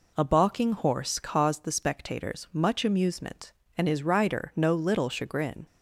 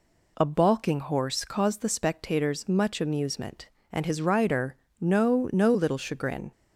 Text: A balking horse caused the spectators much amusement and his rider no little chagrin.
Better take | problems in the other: first | pauses between "rider" and "no"; slight; at 4.7 s; 0.24 s long // says "no" twice; at 5.5 s

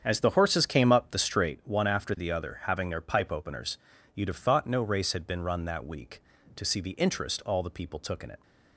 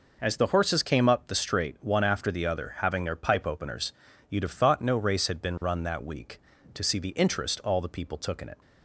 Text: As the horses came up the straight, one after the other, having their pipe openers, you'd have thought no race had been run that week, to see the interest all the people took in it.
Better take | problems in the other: second | starts louder than the rest; strong; until 1.6 s; 7.5 dB

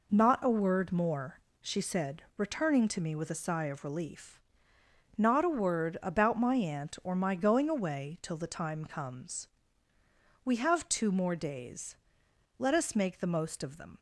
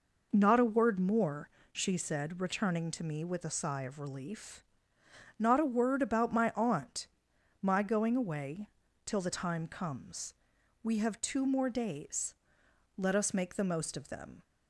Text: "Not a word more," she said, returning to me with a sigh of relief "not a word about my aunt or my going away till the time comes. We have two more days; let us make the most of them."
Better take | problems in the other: first | pauses between "relief" and "not"; noticeable; at 4.6 s; 0.76 s long; noticeable in the first // skips "or"; at 7.3 s // pauses between "away" and "till"; at 8.6 s; 0.38 s long

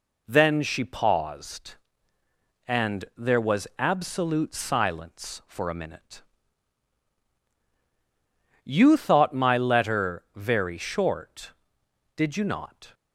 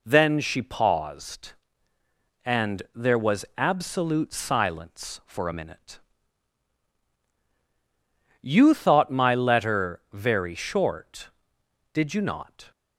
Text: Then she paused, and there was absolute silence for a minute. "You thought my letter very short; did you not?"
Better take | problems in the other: neither | none

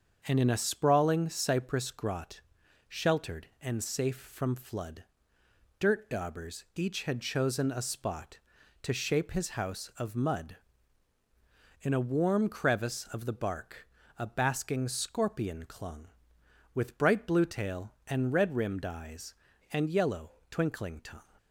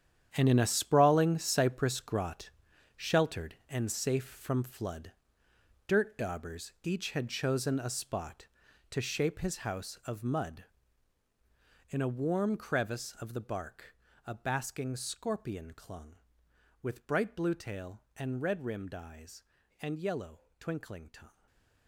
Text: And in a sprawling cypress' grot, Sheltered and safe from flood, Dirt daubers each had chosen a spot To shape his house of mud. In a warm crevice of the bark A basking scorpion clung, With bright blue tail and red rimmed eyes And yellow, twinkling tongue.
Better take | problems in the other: first | gets quieter; strong; throughout; 12.5 dB // starts louder than the rest; strong; until 1.3 s; 9.5 dB; also in the first // pauses between "bark" and "A"; slight; at 13.9 s; 0.30 s long; slight in the first // stays silent after the last word; slight; from 21.2 s on; 0.6 s long

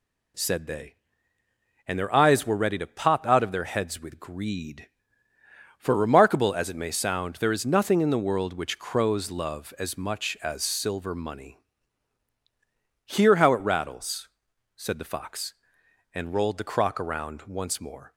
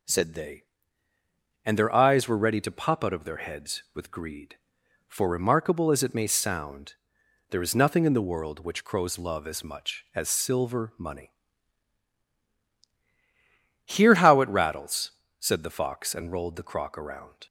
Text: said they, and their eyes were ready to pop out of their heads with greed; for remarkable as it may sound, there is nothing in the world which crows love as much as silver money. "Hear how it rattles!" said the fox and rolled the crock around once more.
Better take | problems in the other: first | stops before "once more"; at 17.4 s

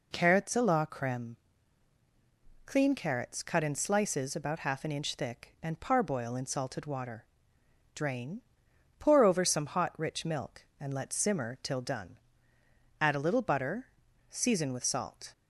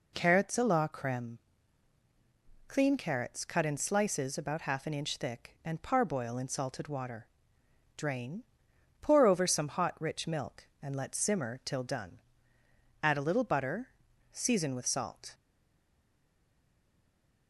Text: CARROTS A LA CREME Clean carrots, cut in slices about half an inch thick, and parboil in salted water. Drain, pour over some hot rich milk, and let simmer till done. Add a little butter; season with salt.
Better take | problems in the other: first | pauses between "CREME" and "Clean"; strong; at 1.3 s; 1.3 s long; strong in the first // stays silent after the last word; from 15.3 s on; 2.1 s long

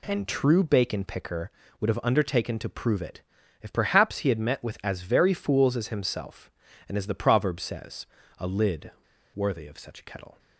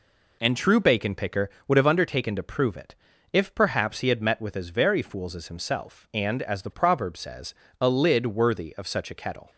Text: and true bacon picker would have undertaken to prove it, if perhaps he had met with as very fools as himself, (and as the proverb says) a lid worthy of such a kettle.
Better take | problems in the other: second | pauses between "lid" and "worthy"; at 8.9 s; 0.44 s long

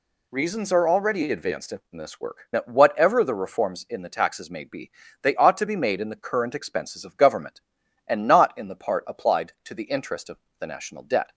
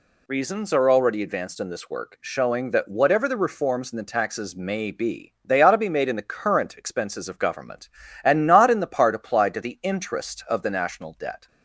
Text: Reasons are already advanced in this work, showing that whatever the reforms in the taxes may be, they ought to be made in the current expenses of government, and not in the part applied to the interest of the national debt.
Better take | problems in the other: second | skips "showing"; at 2.5 s // pauses between "of" and "the"; slight; at 10.3 s; 0.20 s long

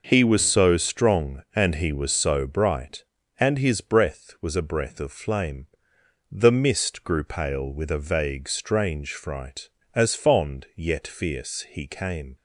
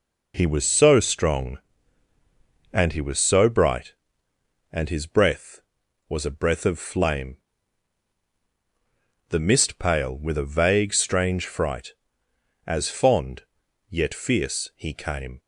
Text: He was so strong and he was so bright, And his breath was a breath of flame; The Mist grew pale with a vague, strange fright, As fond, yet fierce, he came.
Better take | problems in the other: first | skips "grew"; at 9.7 s

